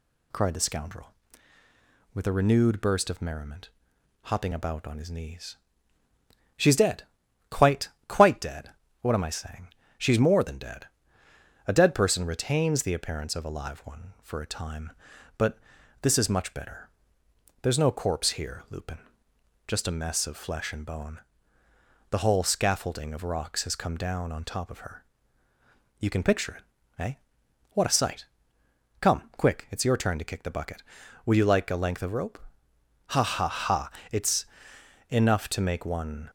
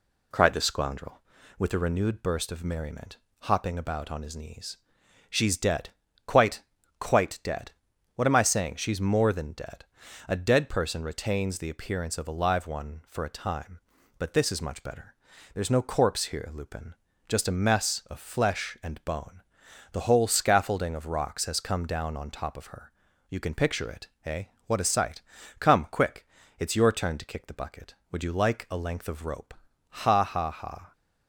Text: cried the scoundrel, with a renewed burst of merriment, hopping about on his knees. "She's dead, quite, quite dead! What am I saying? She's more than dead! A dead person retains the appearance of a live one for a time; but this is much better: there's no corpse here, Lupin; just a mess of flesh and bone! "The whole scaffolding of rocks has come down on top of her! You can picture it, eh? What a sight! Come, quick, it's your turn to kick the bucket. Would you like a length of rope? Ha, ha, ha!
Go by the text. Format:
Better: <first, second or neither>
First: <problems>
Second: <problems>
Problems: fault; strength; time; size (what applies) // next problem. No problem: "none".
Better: second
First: pauses between "but" and "this"; at 15.5 s; 0.44 s long // goes on to say "It's enough to make one"; strong; from 34.1 s on; 2.1 s long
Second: none